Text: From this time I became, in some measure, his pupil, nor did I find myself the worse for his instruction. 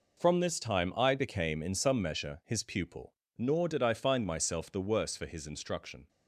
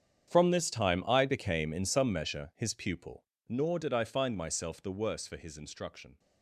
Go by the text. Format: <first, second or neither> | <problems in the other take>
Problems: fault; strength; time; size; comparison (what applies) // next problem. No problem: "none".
first | gets quieter; strong; throughout; 16.5 dB